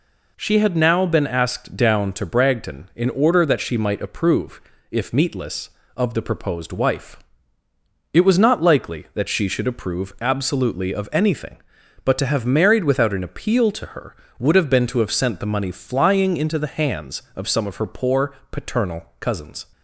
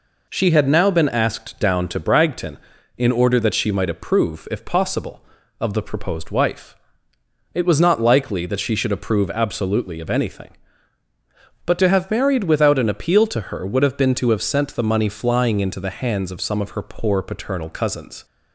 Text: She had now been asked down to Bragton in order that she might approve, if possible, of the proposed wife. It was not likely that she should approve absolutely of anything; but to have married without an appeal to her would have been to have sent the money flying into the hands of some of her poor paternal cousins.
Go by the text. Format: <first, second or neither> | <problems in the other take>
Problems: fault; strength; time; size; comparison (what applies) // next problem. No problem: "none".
second | says "meatless" for "possible"; at 5.1 s // pauses between "poor" and "paternal"; slight; at 18.3 s; 0.16 s long // pauses between "paternal" and "cousins"; slight; at 19.0 s; 0.16 s long